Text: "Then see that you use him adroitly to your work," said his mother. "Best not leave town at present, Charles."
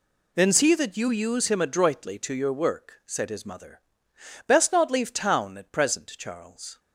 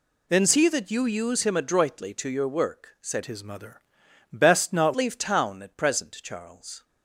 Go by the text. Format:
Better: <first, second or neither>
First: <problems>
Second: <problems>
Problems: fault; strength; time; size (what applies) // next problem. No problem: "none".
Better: first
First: none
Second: changes voice from "his" to "not"; from 3.2 to 4.9 s; 1.7 s long